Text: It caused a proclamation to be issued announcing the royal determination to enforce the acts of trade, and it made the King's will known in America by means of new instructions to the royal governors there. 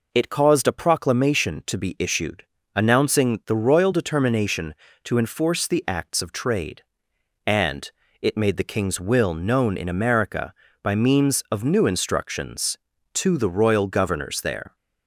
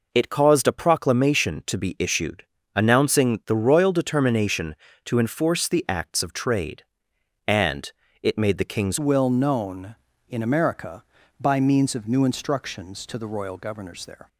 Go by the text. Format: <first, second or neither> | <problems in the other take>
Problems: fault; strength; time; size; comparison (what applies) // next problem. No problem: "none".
first | pauses between "issued" and "announcing"; slight; at 2.4 s; 0.32 s long; slight in the first // pauses between "and" and "it"; slight; at 7.9 s; 0.32 s long; slight in the first // changes voice at "will"; from 8.9 s on; 5.3 s long